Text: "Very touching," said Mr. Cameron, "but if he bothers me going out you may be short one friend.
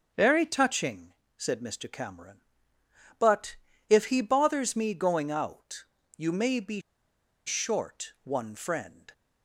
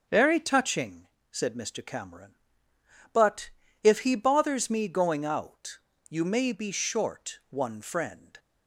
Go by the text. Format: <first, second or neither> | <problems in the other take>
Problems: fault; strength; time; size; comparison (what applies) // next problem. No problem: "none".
second | starts louder than the rest; until 1.4 s; 6.5 dB; also in the second // pauses between "but" and "if"; slight; at 3.5 s; 0.34 s long; slight in the second // pauses between "out" and "you"; slight; at 5.8 s; 0.30 s long; slight in the second // pauses between "be" and "short"; noticeable; at 6.7 s; 0.66 s long